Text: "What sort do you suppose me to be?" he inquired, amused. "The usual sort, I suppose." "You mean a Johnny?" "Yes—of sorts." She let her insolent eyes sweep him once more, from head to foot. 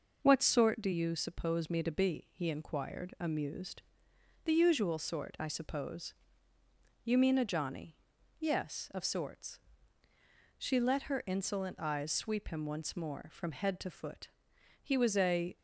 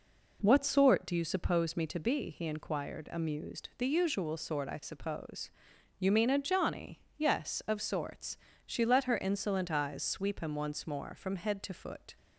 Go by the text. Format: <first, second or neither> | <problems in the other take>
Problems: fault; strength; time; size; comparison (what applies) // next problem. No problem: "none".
second | goes on to say "He was a"; noticeable; from 14.8 s on; 0.76 s long